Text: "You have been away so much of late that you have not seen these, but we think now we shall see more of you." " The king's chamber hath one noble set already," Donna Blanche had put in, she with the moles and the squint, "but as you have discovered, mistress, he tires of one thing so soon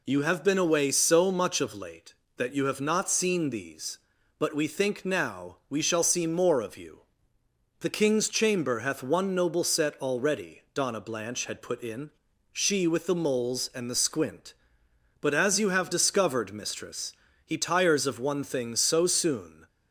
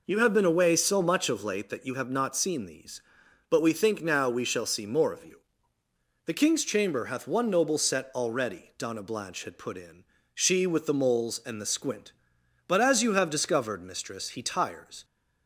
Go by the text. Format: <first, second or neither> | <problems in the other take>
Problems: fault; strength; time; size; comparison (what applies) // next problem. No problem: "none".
first | stops before "of one thing so soon"; at 15.0 s